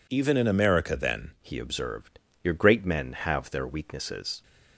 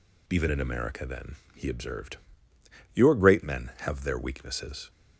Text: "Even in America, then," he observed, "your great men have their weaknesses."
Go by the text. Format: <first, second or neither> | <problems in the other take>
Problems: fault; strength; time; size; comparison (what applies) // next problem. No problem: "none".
second | changes voice at "he"; from 1.4 s on; 3.0 s long